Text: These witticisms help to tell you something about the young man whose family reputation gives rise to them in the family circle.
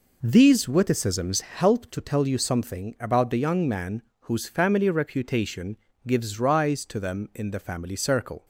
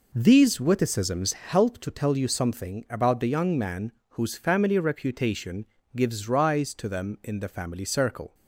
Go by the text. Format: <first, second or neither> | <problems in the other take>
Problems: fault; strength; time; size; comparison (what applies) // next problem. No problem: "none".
neither | pauses between "man" and "whose"; slight; the same in both // pauses between "reputation" and "gives"; slight; the same in both